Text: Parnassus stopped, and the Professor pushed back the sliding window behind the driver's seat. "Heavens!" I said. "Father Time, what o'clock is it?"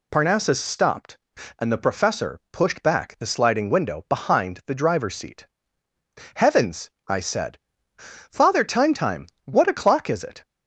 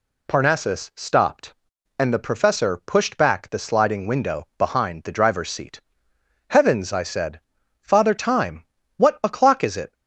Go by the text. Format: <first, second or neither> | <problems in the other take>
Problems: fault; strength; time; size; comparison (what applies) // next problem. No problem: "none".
second | says "Time" twice; at 8.9 s